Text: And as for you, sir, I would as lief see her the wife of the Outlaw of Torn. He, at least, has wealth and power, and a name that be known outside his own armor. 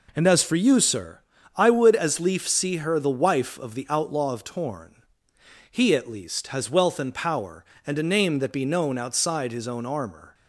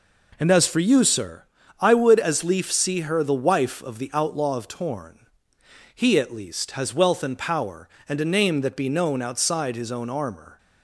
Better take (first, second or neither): neither